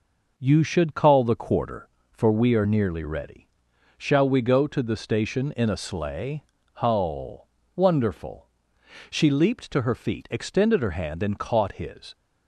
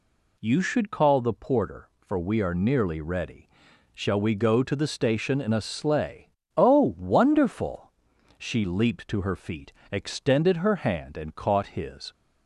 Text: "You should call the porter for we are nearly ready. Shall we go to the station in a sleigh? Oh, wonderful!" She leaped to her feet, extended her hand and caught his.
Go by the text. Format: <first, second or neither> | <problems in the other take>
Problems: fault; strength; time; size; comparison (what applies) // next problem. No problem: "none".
second | says "quarter" for "porter"; at 1.3 s